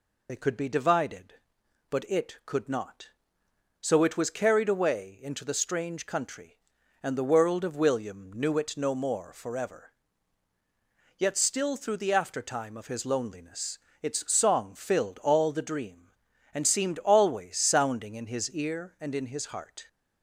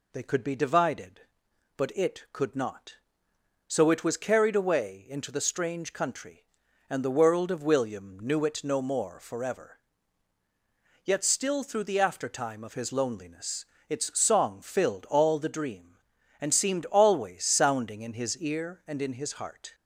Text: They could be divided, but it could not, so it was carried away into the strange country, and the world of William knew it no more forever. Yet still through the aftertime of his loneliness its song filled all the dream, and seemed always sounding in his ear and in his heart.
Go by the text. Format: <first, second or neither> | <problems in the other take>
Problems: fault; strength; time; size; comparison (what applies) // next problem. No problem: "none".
second | loses the start of "They"; at 0.2 s; 40 ms // pauses between "loneliness" and "its"; slight; at 13.7 s; 0.24 s long; slight in the second